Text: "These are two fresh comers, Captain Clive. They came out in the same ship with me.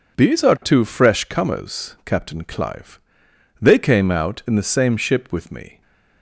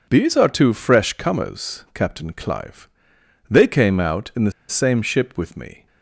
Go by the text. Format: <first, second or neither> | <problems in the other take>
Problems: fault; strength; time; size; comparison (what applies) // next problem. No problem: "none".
first | pauses between "the" and "same"; slight; at 4.5 s; 0.17 s long